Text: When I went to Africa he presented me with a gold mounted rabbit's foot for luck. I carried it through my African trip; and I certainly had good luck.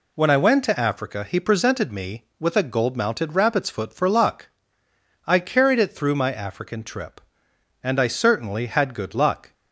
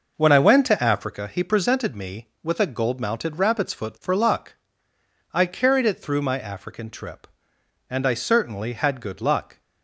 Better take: first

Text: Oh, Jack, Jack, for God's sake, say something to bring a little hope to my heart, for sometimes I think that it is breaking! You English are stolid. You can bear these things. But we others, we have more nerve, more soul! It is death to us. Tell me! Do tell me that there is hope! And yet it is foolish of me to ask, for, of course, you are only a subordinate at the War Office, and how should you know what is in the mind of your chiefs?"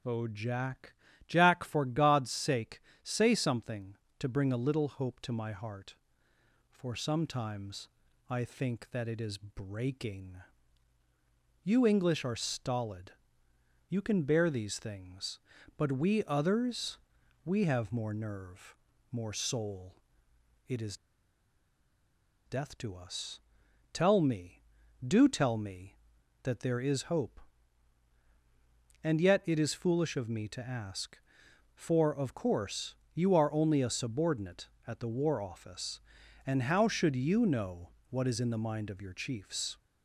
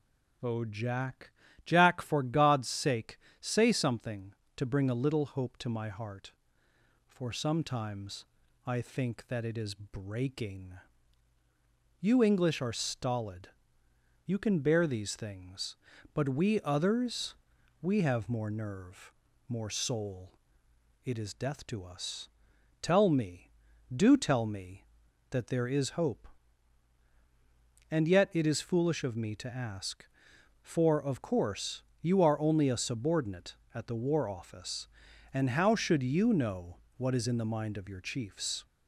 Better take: second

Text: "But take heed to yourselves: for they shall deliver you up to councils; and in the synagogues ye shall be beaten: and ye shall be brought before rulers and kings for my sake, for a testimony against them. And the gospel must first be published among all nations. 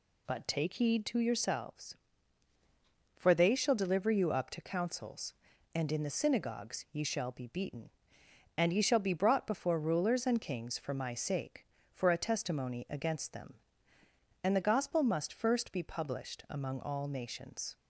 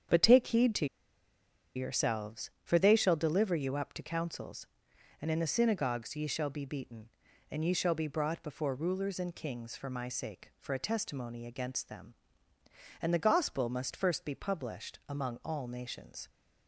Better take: first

